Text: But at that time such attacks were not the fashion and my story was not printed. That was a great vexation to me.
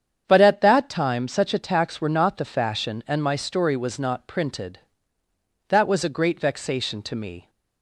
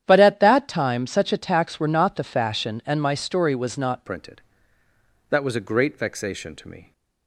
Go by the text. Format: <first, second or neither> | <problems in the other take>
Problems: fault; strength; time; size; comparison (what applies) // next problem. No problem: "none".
first | starts louder than the rest; strong; until 1.0 s; 10 dB; strong in the first // changes voice at "printed"; from 4.0 s on; 2.9 s long